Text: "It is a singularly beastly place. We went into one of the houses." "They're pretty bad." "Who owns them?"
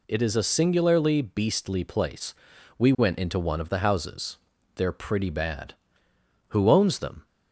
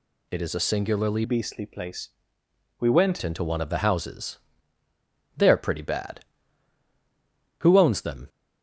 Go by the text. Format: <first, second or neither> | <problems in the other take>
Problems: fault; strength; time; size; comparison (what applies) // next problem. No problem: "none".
first | changes voice from "beastly" to "went"; from 1.2 to 3.2 s; 2.0 s long